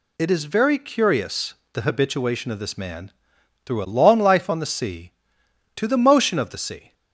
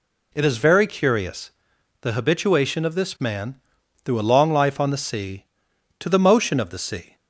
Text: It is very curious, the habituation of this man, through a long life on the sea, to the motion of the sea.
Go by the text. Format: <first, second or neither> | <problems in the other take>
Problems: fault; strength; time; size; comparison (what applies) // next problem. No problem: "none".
neither | none